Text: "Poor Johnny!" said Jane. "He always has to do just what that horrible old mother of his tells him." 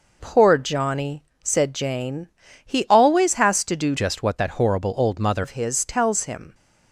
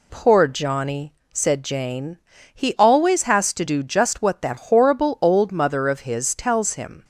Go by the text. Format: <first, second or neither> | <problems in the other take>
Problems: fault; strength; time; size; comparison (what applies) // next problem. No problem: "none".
second | changes voice from "just" to "mother"; from 3.9 to 5.4 s; 1.5 s long